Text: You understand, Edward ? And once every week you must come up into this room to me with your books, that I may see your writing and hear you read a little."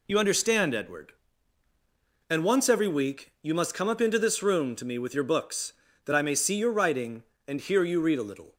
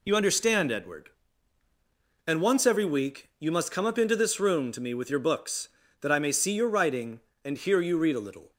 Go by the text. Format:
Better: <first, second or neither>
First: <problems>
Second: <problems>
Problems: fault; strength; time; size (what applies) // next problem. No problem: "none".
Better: neither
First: none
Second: none